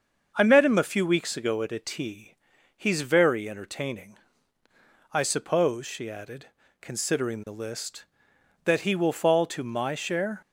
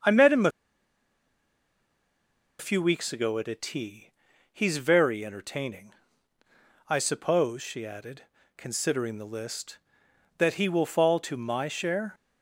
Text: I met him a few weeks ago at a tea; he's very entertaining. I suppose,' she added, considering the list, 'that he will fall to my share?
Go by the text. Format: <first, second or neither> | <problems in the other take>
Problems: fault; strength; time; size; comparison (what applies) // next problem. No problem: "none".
first | starts louder than the rest; until 3.1 s; 6.5 dB; also in the first // pauses between "a" and "few"; strong; at 0.5 s; 2.0 s long